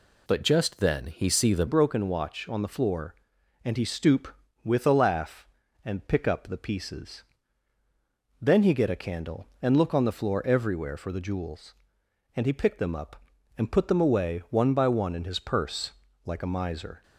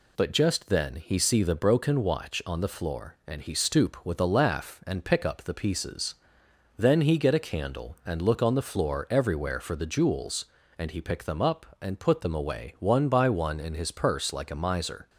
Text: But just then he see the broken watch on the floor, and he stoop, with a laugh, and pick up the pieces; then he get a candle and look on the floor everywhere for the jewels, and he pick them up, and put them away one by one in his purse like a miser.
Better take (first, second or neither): second